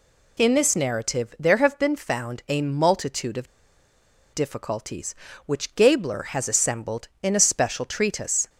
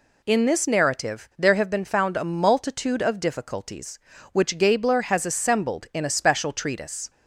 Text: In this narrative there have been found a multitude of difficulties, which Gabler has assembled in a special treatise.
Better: second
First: pauses between "of" and "difficulties"; noticeable; at 3.4 s; 0.87 s long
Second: none

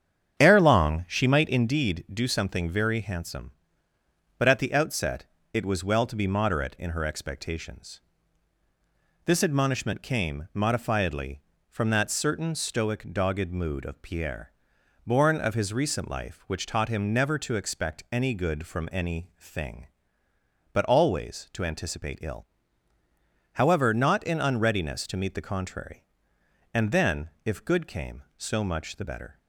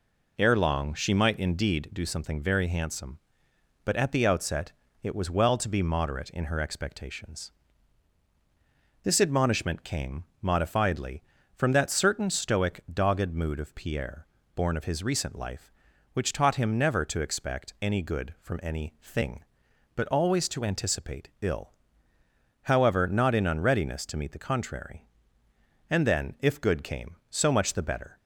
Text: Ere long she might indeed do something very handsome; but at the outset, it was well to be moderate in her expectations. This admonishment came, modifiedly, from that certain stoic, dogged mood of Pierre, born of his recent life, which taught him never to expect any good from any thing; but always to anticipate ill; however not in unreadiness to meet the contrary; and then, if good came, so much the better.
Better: second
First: starts louder than the rest; strong; until 1.7 s; 8.5 dB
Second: none

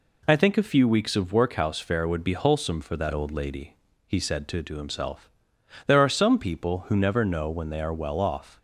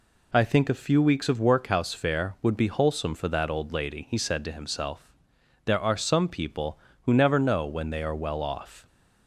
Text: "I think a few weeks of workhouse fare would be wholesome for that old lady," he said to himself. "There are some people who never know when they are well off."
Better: second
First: says "to" twice; at 4.6 s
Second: none

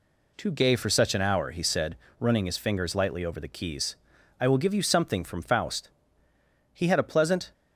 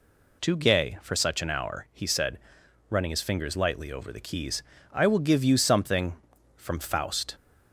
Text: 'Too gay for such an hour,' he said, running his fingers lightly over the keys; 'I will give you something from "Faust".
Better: second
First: goes on to say "He had a pleasant"; noticeable; from 6.7 s on; 0.78 s long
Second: none

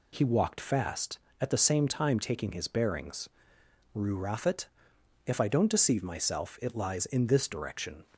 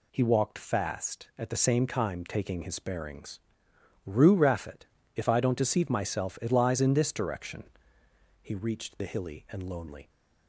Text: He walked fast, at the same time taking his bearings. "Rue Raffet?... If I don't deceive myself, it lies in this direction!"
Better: first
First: none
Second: goes on to say "He reached the hilly and lonely"; strong; from 8.4 s on; 1.6 s long

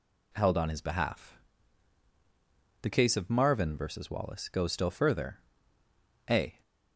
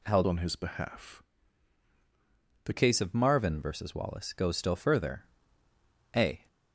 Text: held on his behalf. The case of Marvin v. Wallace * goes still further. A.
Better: first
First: none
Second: changes voice from "on" to "The"; from 0.2 to 2.7 s; 2.5 s long

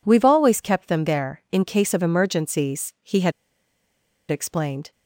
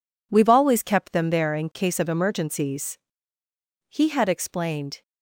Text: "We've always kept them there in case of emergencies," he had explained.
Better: second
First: pauses between "had" and "explained"; at 3.3 s; 0.98 s long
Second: none

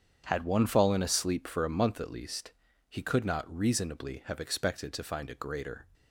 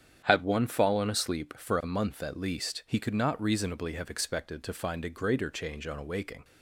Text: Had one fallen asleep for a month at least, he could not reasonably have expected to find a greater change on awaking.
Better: second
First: starts louder than the rest; strong; until 1.2 s; 7.5 dB // stops before "change on awaking"; at 5.9 s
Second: starts louder than the rest; strong; until 1.2 s; 9 dB

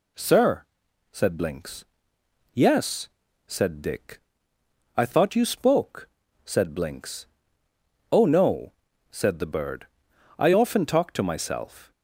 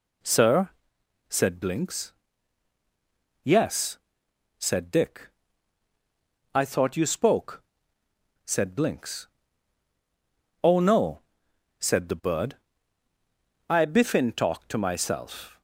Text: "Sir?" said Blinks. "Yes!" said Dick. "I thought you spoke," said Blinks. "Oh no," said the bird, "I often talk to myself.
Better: first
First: none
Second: says "biffin" for "often"; at 13.8 s

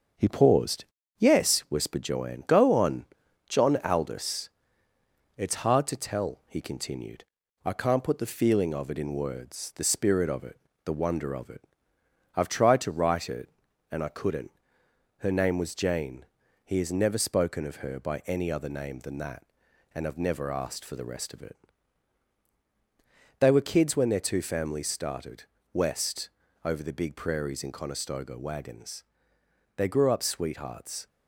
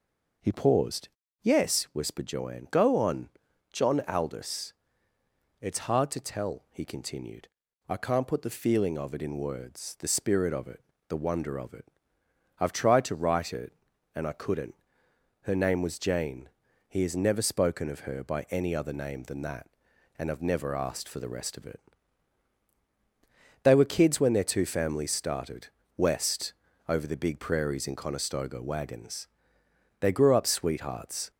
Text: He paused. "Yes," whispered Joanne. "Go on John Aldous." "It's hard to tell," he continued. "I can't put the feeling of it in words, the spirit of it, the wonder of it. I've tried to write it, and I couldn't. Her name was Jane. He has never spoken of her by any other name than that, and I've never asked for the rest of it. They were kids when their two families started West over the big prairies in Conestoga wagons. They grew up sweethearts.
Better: second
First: gets quieter; noticeable; throughout; 4 dB // pauses between "on" and "John"; at 3.0 s; 0.42 s long // pauses between "started" and "West"; slight; at 25.4 s; 0.28 s long // pauses between "West" and "over"; slight; at 26.3 s; 0.34 s long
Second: pauses between "on" and "John"; at 3.2 s; 0.42 s long // pauses between "started" and "West"; slight; at 25.6 s; 0.28 s long // pauses between "West" and "over"; slight; at 26.5 s; 0.34 s long

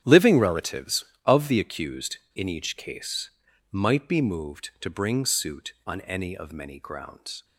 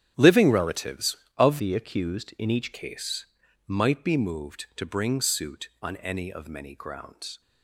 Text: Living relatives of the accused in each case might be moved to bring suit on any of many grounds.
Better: first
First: starts louder than the rest; strong; until 1.0 s; 9 dB // pauses between "case" and "might"; at 3.3 s; 0.42 s long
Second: starts louder than the rest; strong; until 1.1 s; 10 dB // changes voice from "the" to "each"; from 1.5 to 2.7 s; 1.2 s long // pauses between "case" and "might"; at 3.2 s; 0.42 s long

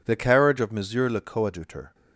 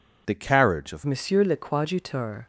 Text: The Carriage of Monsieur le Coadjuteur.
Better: first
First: none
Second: changes voice at "Monsieur"; from 1.0 s on; 1.4 s long

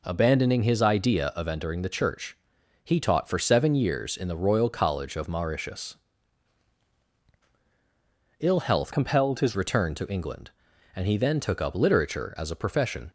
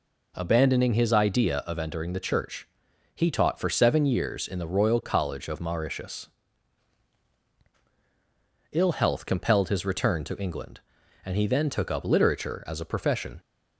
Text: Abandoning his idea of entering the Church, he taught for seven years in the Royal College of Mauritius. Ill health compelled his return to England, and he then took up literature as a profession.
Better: second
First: changes voice from "compelled" to "his"; from 8.9 to 9.5 s; 0.6 s long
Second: none

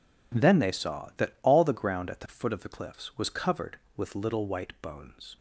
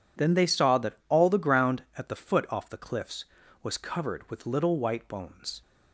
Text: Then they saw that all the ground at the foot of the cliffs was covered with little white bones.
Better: first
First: none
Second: says "off" for "of"; at 2.4 s

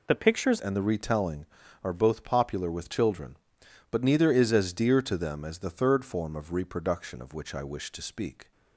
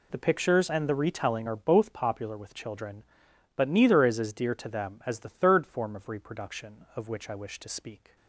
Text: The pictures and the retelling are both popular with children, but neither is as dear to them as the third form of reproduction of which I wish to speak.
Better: second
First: changes voice at "and"; from 0.5 s on; 8.0 s long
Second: none

